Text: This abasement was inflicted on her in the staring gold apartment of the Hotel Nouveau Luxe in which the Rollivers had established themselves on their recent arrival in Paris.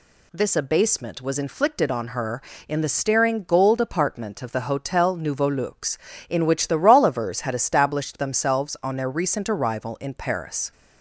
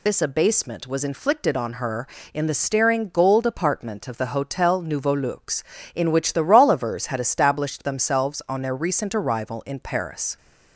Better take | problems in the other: first | loses the start of "This"; at 0.0 s; 90 ms

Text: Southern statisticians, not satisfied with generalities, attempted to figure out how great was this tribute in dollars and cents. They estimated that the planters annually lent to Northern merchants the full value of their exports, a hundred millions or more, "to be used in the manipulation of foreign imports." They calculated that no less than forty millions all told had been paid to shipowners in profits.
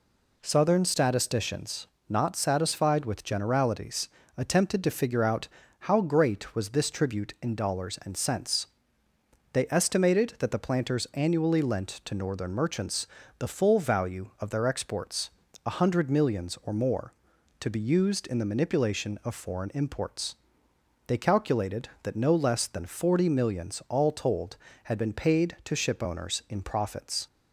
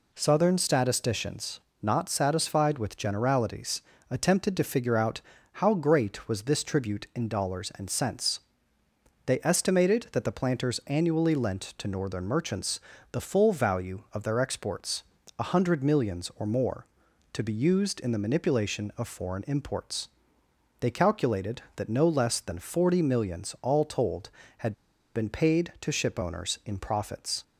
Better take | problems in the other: first | pauses between "out" and "how"; slight; at 5.2 s; 0.32 s long; slight in the first // pauses between "merchants" and "the"; slight; at 12.7 s; 0.34 s long; slight in the first // pauses between "had" and "been"; at 24.7 s; 0.41 s long

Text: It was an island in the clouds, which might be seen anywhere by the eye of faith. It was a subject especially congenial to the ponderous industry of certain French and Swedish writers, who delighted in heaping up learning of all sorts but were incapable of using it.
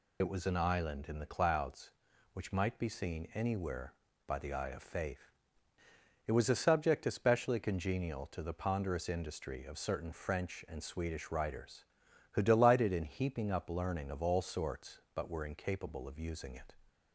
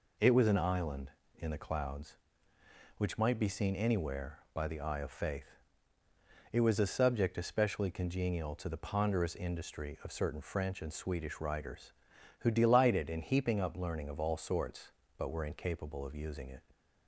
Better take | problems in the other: second | loses the start of "It"; at 0.2 s; 55 ms

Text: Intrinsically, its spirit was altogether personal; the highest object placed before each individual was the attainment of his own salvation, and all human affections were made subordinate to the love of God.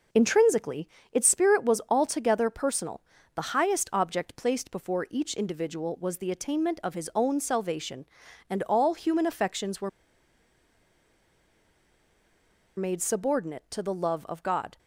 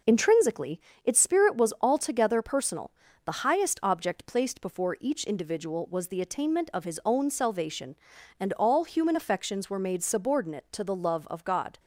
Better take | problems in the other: second | pauses between "were" and "made"; strong; at 9.8 s; 2.8 s long

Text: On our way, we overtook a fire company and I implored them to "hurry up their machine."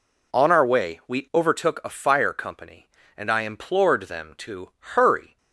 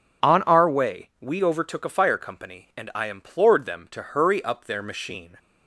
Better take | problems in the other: second | stops before "up their machine"; at 5.3 s

